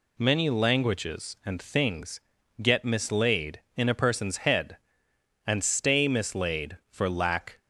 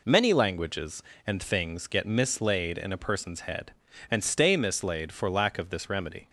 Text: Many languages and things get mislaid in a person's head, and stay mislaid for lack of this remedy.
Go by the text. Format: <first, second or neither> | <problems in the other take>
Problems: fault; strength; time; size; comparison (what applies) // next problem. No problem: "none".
second | pauses between "things" and "get"; at 2.2 s; 0.38 s long // stops before "of this remedy"; at 7.5 s